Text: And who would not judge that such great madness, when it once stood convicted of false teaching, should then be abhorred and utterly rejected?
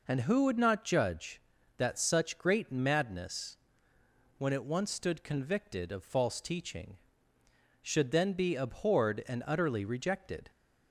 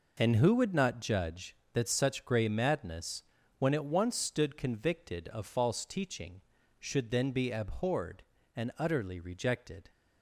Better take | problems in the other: first | says "grey" for "great"; at 2.2 s

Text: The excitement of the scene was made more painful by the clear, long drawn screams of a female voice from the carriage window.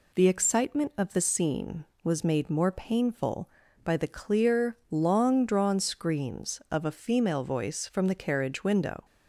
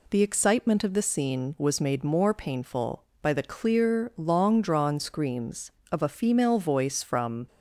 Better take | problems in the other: first | stops before "the carriage window"; at 7.4 s

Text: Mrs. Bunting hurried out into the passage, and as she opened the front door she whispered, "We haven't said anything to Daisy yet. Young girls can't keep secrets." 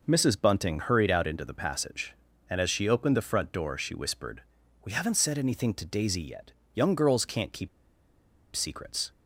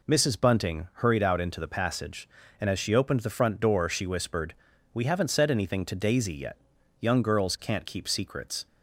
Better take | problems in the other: second | pauses between "keep" and "secrets"; noticeable; at 7.6 s; 0.85 s long

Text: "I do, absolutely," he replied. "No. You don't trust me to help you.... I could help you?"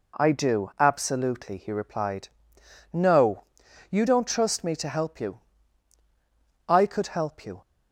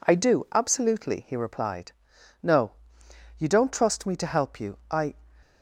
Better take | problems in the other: first | stops before "could help you"; at 5.4 s

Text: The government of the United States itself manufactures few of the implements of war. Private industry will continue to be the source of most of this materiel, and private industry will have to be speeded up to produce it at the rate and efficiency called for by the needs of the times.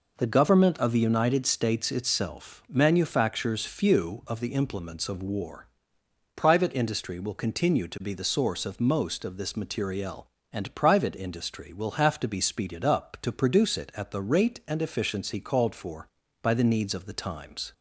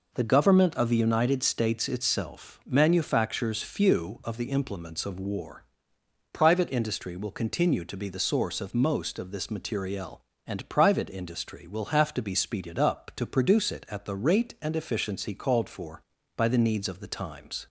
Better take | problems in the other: neither | none

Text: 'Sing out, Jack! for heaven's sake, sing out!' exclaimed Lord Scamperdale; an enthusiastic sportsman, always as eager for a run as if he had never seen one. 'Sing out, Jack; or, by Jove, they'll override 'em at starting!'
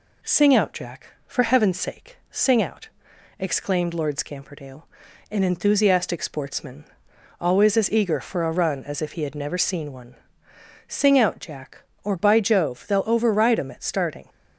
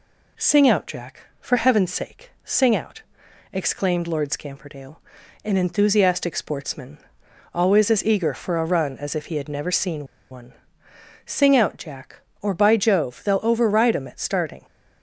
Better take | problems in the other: first | pauses between "seen" and "one"; slight; at 10.0 s; 0.26 s long

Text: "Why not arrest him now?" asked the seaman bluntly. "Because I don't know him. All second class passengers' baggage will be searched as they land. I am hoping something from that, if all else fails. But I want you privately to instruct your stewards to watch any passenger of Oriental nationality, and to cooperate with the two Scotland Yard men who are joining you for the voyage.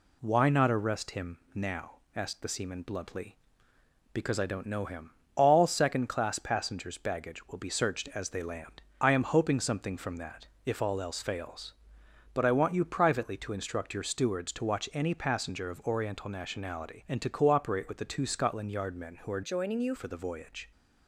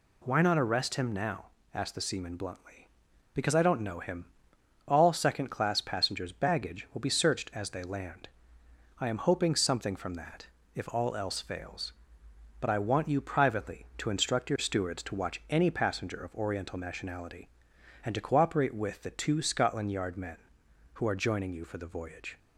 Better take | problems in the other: second | pauses between "him" and "now"; slight; at 1.3 s; 0.16 s long // changes voice from "joining" to "you"; from 19.4 to 19.9 s; 0.5 s long

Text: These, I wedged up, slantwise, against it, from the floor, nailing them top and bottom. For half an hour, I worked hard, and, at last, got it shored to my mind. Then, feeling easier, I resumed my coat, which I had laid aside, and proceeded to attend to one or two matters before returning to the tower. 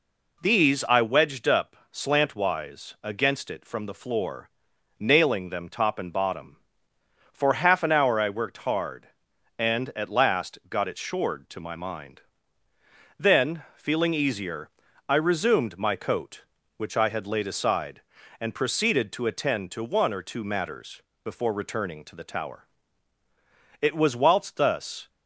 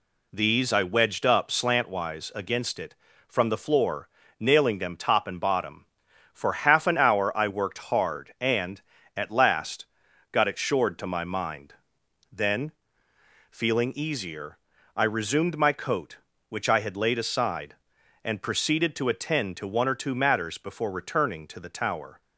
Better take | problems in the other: second | pauses between "matters" and "before"; slight; at 21.0 s; 0.24 s long // goes on to say "It was whilst thus"; noticeable; from 23.8 s on; 1.2 s long

